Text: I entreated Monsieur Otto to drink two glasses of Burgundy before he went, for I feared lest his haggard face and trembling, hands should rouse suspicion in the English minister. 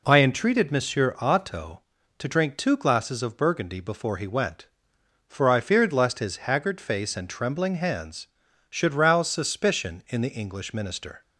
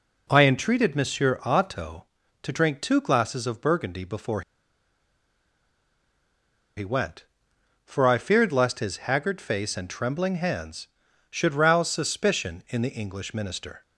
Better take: first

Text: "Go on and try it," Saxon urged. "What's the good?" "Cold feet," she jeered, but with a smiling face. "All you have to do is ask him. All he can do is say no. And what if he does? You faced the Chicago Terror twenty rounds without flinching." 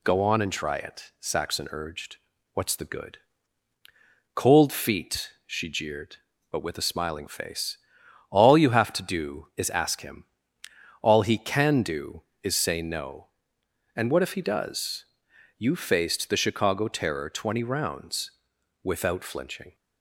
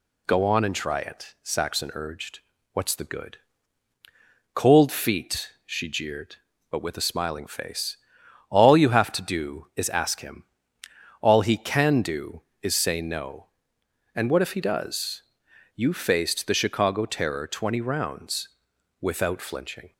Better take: neither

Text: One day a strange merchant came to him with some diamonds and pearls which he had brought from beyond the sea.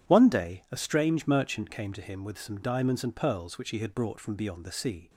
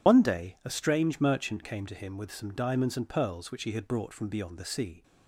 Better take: first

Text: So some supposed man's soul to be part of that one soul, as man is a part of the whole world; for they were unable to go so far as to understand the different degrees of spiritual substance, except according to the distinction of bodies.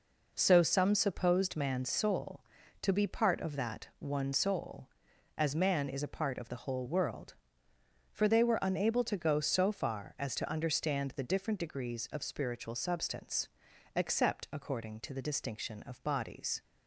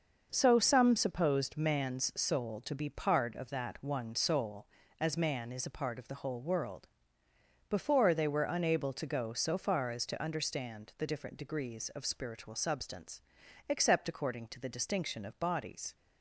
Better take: first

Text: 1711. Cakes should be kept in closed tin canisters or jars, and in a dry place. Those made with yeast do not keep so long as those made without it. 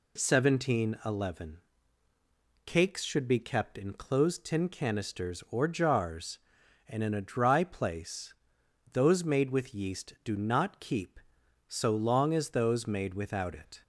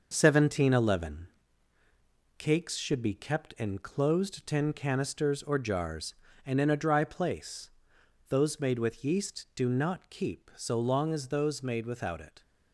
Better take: first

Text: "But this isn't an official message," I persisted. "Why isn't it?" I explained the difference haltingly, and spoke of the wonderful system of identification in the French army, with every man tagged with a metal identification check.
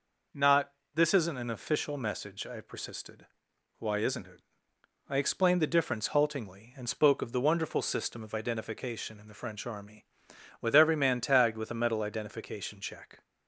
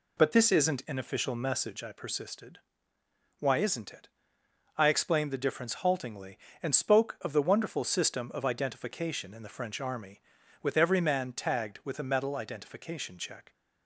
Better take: second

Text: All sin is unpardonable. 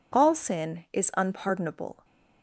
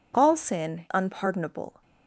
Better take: first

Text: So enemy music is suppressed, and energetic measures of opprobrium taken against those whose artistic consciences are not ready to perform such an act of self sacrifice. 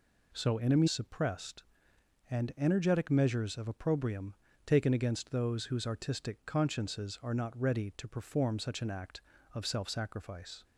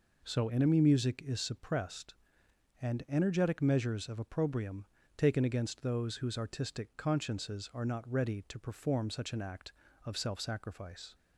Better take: second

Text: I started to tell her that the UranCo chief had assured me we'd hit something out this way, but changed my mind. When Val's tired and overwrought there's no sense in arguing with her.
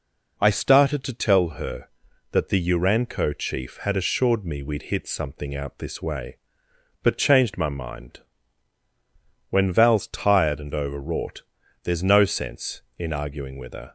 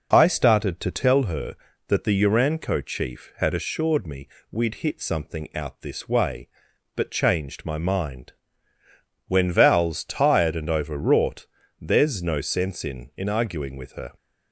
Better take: first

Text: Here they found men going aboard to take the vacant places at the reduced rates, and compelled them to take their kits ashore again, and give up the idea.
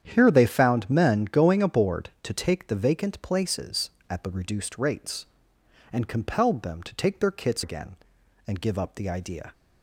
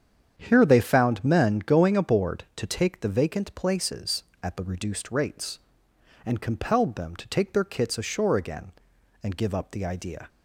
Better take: second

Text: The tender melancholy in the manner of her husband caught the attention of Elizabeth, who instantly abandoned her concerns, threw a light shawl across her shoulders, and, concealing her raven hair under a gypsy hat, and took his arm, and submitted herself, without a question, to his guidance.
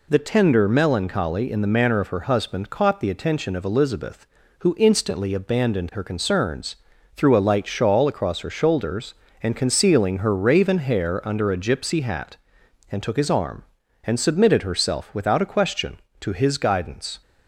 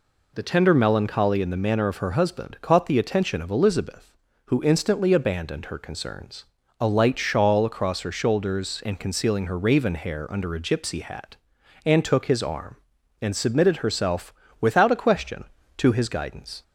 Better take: first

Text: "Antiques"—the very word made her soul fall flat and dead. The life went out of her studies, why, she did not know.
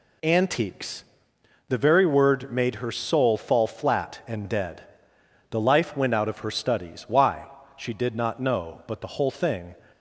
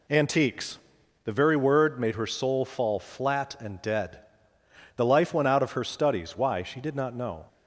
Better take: second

